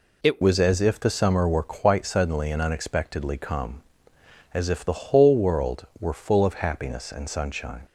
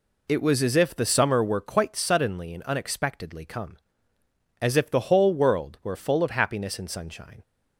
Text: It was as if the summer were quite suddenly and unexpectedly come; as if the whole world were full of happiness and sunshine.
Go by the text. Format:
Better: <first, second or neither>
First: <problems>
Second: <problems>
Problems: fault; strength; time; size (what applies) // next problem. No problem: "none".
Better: second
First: changes voice at "was"; from 0.4 s on; 7.4 s long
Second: none